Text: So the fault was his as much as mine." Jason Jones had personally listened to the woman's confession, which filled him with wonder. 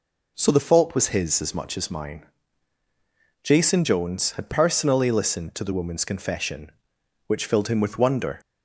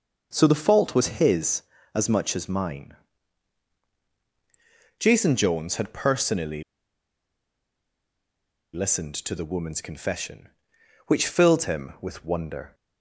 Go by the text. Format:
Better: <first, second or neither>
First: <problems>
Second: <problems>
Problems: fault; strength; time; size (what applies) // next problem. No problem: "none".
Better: first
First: none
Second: pauses between "personally" and "listened"; strong; at 6.6 s; 2.1 s long